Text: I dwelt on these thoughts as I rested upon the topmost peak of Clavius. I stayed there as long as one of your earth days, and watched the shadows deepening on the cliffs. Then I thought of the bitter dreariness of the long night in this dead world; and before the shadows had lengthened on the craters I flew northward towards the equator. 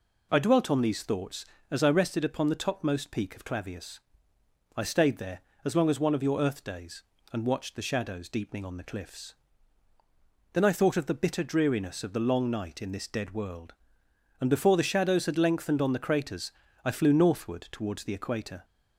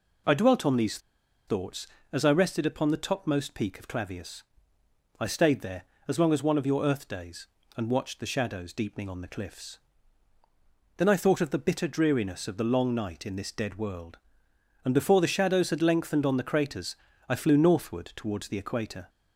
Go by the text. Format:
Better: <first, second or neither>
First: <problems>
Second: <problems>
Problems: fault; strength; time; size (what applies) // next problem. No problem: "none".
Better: first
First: pauses between "craters" and "I"; slight; at 16.5 s; 0.34 s long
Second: pauses between "these" and "thoughts"; noticeable; at 0.9 s; 0.49 s long // pauses between "craters" and "I"; slight; at 16.9 s; 0.34 s long